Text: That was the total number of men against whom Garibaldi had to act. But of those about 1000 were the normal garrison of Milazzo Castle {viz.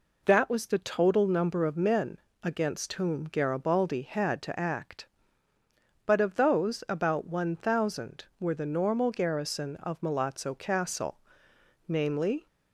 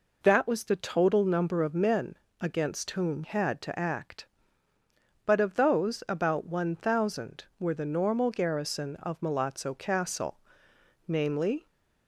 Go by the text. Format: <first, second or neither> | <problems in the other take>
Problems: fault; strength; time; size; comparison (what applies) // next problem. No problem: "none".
first | pauses between "men" and "against"; slight; at 2.1 s; 0.24 s long; slight in the first // skips "Garibaldi"; at 3.2 s